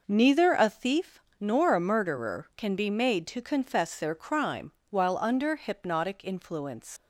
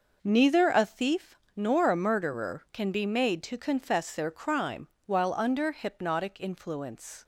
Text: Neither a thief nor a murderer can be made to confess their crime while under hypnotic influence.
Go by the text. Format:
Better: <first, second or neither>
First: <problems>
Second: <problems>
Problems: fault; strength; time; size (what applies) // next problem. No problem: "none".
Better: second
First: pauses between "thief" and "nor"; slight; at 1.2 s; 0.18 s long // pauses between "crime" and "while"; slight; at 4.7 s; 0.18 s long // leaves "influence" unfinished; at 6.9 s; 115 ms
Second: pauses between "thief" and "nor"; slight; at 1.3 s; 0.18 s long // pauses between "crime" and "while"; slight; at 4.8 s; 0.18 s long